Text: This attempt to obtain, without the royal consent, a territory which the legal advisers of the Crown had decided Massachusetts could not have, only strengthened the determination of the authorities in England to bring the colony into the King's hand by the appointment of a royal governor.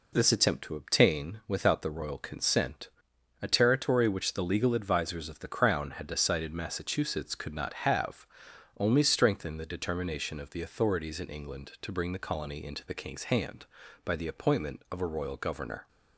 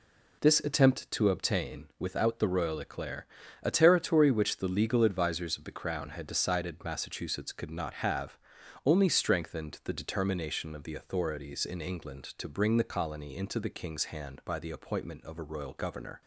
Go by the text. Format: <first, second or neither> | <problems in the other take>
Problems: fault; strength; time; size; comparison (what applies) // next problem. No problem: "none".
first | says "eclair" for "consent"; at 2.7 s